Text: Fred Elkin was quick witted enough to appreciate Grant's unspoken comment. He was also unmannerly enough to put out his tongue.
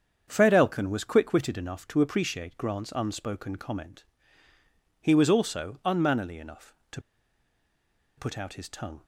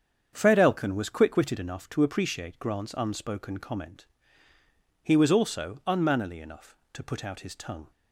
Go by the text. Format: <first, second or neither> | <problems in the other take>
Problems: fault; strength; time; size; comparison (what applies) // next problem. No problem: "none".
second | starts louder than the rest; strong; until 1.2 s; 7.5 dB; strong in the second // pauses between "to" and "put"; at 7.0 s; 1.1 s long